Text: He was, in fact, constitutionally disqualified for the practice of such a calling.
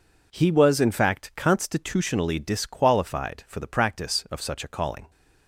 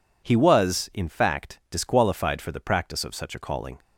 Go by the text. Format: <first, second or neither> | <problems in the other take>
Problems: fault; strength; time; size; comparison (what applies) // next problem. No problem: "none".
first | skips "constitutionally"; at 1.6 s